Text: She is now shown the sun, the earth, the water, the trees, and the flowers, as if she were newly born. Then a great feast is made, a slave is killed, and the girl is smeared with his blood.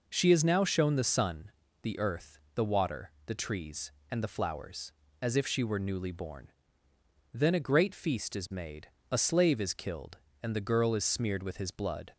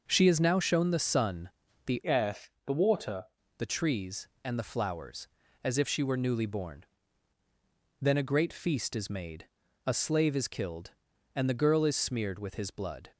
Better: first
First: none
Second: changes voice from "earth" to "water"; from 2.0 to 3.2 s; 1.2 s long

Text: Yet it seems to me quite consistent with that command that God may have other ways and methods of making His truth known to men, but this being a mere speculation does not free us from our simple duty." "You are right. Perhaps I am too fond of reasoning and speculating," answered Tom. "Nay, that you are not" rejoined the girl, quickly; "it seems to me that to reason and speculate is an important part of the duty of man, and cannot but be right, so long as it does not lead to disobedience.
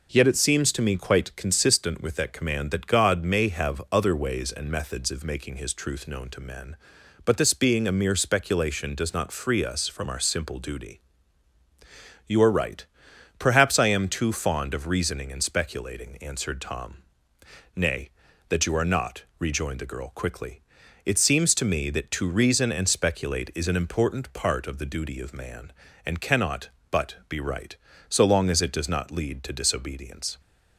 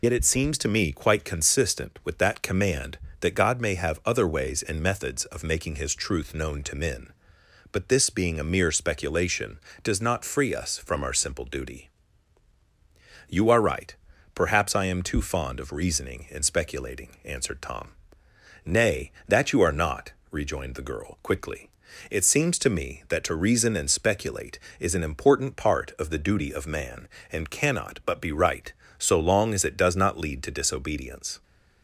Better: first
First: pauses between "not" and "rejoined"; slight; at 19.2 s; 0.16 s long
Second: loses the start of "Yet"; at 0.0 s; 80 ms // pauses between "not" and "rejoined"; slight; at 20.1 s; 0.18 s long

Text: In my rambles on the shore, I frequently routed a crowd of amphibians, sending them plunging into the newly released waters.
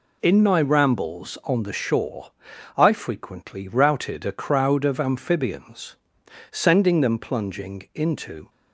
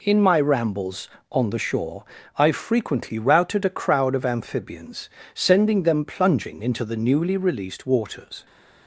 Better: second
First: stops before "the newly released waters"; at 8.4 s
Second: none

